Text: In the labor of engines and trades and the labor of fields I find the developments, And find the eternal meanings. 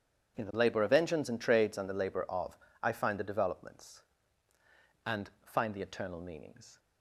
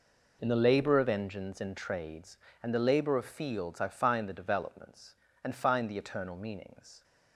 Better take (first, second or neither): second